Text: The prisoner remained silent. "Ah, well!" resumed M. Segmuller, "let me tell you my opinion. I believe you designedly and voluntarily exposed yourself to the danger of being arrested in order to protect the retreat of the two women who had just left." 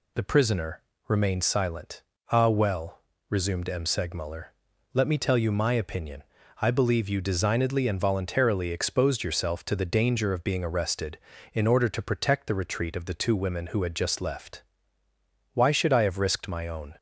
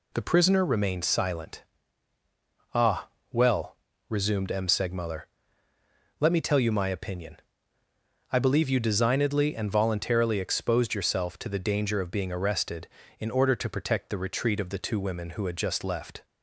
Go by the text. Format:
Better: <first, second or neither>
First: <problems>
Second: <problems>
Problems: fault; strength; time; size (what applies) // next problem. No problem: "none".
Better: second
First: pauses between "prisoner" and "remained"; slight; at 0.8 s; 0.24 s long // goes on to say "Why should I have risked my own"; from 15.5 s on; 1.4 s long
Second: none